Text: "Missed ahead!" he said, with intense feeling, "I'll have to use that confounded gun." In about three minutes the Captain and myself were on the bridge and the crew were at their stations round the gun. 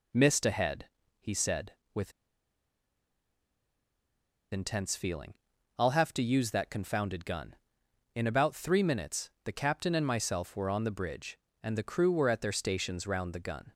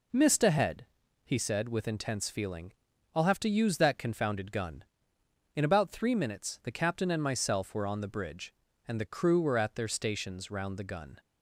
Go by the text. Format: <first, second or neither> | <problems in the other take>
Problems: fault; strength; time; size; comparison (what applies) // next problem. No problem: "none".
second | pauses between "with" and "intense"; strong; at 2.1 s; 2.4 s long // pauses between "minutes" and "the"; slight; at 9.2 s; 0.16 s long